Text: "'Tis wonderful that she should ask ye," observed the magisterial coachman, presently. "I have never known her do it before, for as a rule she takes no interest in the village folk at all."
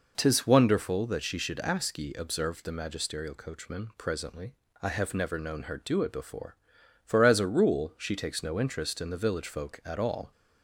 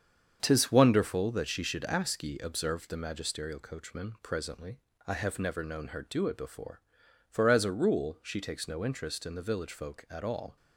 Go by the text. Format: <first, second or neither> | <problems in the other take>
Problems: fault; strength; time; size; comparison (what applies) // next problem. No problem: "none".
first | gets quieter; throughout; 7 dB